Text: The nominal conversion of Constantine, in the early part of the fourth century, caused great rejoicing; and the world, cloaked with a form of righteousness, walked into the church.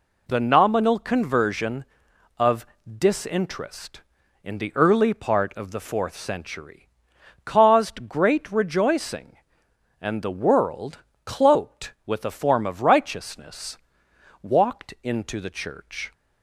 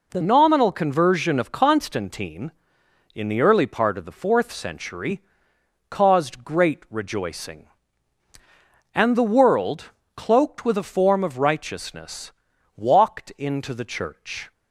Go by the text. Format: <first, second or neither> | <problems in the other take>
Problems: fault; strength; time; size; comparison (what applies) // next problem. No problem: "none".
second | says "Disinterest" for "Constantine"; at 2.9 s